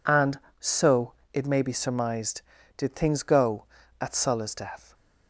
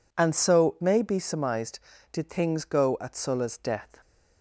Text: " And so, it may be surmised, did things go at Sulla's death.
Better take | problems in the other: first | skips "it"; at 0.7 s

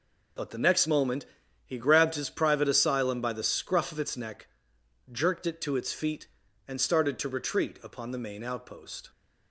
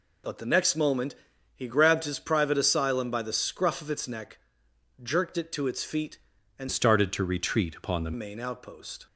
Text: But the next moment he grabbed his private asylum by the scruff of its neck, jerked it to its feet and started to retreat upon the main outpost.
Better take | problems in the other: first | pauses between "moment" and "he"; at 1.1 s; 0.42 s long; also in the first // changes voice from "started" to "the"; from 6.6 to 8.1 s; 1.5 s long

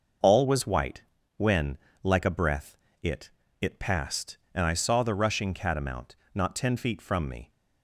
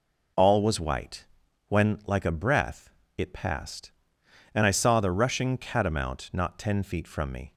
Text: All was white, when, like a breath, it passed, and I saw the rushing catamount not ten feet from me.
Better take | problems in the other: second | says "it" twice; at 3.6 s // pauses between "catamount" and "not"; slight; at 6.1 s; 0.20 s long

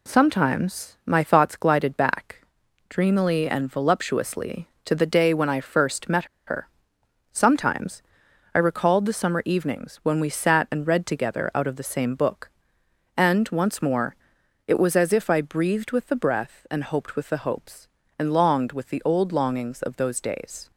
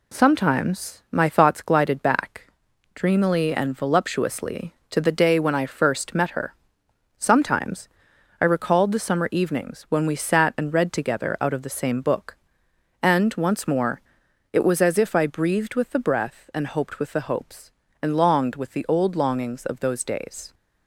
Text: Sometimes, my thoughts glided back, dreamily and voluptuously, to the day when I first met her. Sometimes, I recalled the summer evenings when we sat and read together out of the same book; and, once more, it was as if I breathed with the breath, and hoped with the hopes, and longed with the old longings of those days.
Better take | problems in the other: second | pauses between "met" and "her"; slight; at 6.2 s; 0.22 s long

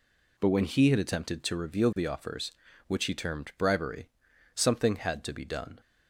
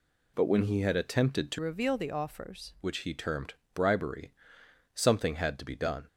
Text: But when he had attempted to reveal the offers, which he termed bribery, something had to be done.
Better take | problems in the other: first | changes voice from "reveal" to "offers"; from 1.5 to 2.7 s; 1.2 s long // pauses between "termed" and "bribery"; slight; at 3.5 s; 0.20 s long

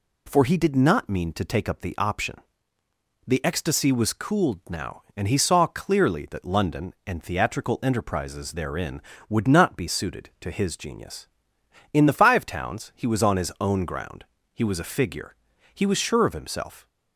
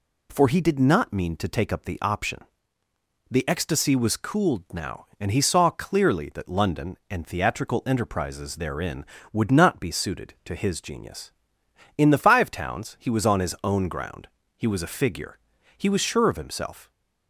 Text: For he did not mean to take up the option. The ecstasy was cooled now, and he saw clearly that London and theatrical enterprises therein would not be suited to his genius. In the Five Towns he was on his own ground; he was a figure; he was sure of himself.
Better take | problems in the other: neither | none

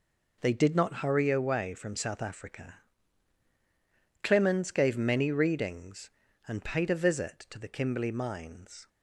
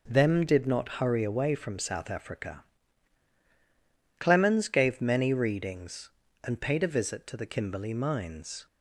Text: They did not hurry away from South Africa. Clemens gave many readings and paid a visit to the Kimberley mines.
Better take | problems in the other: first | says "Them" for "They"; at 0.0 s

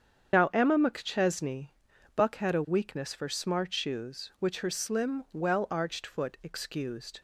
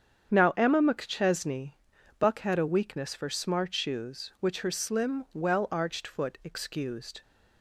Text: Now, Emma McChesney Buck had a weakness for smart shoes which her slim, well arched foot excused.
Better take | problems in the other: second | loses the start of "Now"; at 0.3 s; 70 ms // starts louder than the rest; strong; until 1.3 s; 8 dB; strong in the second // pauses between "McChesney" and "Buck"; noticeable; at 1.6 s; 0.48 s long; noticeable in the second

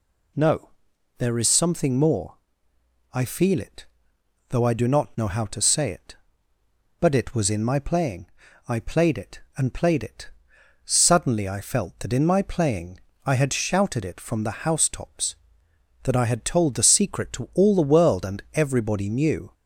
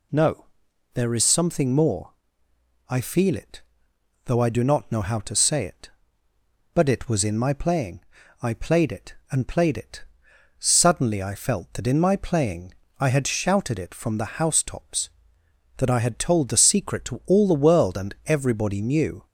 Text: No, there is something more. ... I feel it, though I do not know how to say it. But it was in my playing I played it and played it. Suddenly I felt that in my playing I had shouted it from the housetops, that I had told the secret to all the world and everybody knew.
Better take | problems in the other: neither | pauses between "playing" and "I"; the same in both // pauses between "playing" and "I"; slight; the same in both

